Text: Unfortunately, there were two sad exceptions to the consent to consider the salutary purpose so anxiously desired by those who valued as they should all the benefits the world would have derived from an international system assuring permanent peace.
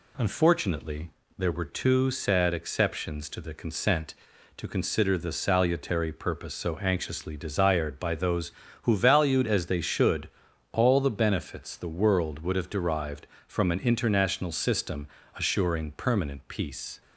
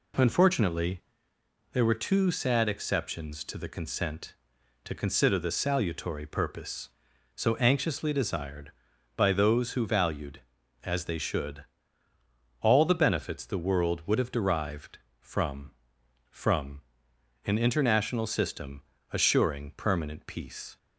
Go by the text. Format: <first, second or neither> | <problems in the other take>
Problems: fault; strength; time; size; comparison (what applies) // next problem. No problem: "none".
first | pauses between "should" and "all"; noticeable; at 11.6 s; 0.98 s long; also in the first // says "from" twice; at 16.2 s // pauses between "system" and "assuring"; slight; at 18.8 s; 0.28 s long; slight in the first